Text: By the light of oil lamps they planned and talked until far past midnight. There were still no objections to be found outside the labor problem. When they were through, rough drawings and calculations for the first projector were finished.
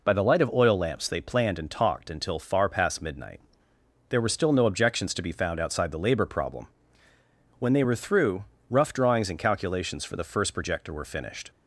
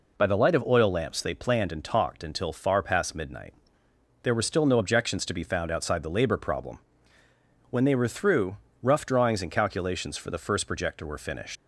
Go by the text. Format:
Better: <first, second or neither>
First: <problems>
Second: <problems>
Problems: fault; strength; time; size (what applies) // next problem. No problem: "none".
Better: first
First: none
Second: leaves "finished" unfinished; at 11.5 s; 75 ms